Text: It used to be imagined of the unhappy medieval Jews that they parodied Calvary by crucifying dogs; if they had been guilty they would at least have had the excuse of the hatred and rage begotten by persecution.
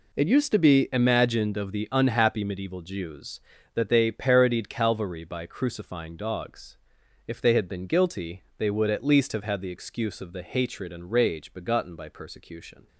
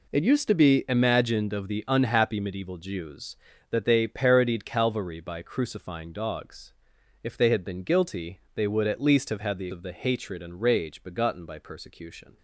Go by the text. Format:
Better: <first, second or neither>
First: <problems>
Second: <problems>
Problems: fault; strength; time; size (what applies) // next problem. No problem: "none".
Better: first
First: none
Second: skips "excuse"; at 9.6 s